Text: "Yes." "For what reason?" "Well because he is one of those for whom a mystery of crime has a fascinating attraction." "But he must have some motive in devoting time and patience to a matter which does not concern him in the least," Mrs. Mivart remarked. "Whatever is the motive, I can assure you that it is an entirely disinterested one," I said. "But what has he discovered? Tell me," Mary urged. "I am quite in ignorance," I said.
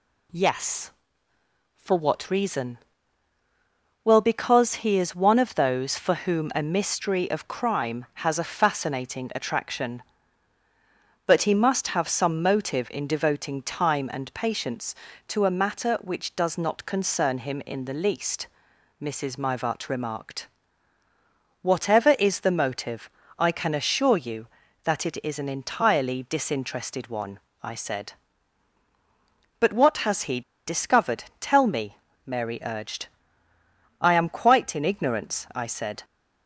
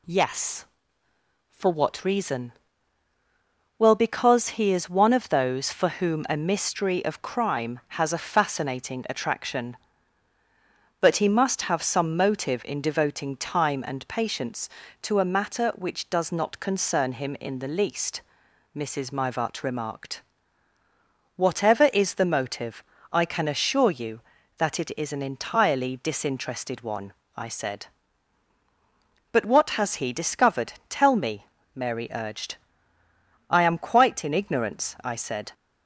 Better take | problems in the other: second | pauses between "he" and "discovered"; slight; at 30.4 s; 0.26 s long

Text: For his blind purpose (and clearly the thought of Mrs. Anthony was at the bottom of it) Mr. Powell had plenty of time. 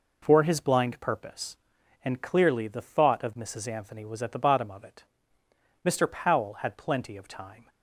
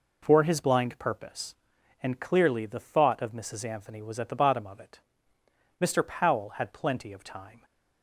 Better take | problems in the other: neither | none

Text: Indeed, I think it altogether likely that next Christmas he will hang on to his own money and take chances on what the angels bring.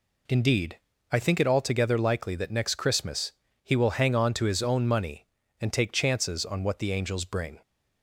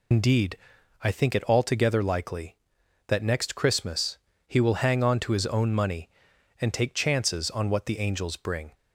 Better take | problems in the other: first | loses the start of "Indeed"; at 0.1 s; 95 ms // pauses between "Christmas" and "he"; slight; at 4.1 s; 0.30 s long; slight in the first

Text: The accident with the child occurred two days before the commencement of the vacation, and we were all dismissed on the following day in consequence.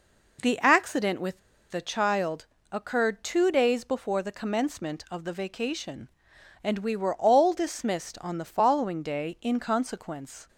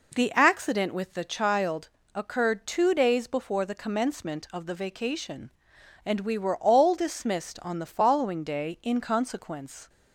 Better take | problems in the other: second | pauses between "with" and "the"; slight; at 1.3 s; 0.31 s long // pauses between "child" and "occurred"; slight; at 2.4 s; 0.24 s long; slight in the second

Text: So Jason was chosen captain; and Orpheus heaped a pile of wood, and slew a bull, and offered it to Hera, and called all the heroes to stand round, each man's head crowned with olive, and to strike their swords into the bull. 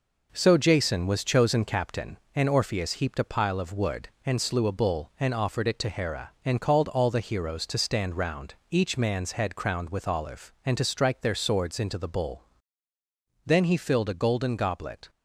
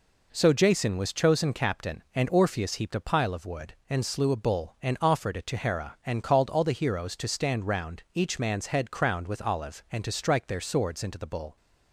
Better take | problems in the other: second | goes on to say "Then he filled a golden goblet"; from 13.4 s on; 1.6 s long

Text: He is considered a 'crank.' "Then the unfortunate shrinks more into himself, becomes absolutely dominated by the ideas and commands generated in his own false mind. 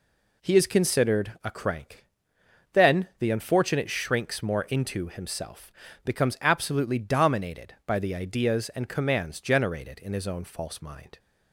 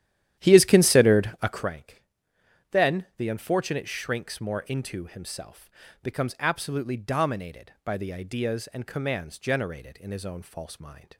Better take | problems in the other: first | starts louder than the rest; strong; until 1.7 s; 11.5 dB

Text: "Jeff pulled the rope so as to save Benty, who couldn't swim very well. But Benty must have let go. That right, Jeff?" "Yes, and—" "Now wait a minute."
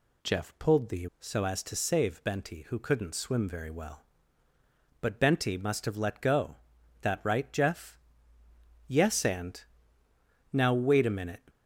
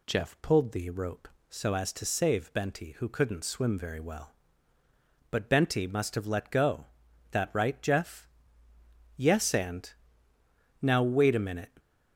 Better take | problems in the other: second | skips "rope"; at 1.1 s

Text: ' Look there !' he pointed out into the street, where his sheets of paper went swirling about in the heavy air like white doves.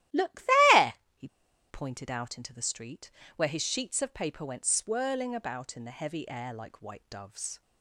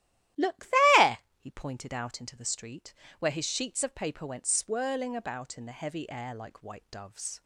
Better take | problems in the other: second | starts louder than the rest; strong; until 1.9 s; 8.5 dB; strong in the second // pauses between "Look" and "there"; slight; at 0.4 s; 0.32 s long; slight in the second // pauses between "he" and "pointed"; at 1.2 s; 0.42 s long

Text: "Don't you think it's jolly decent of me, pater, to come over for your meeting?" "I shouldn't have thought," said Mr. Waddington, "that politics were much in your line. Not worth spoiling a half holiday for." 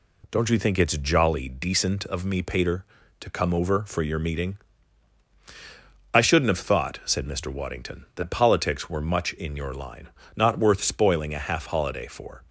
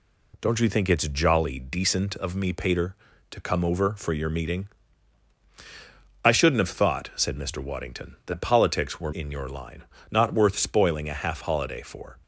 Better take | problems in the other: first | skips "much"; at 9.1 s

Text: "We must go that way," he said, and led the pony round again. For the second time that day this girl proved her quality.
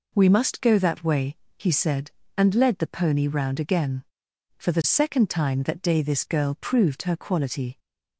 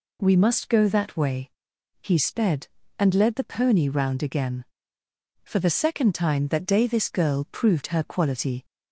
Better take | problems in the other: first | says "sped" for "said"; at 2.1 s

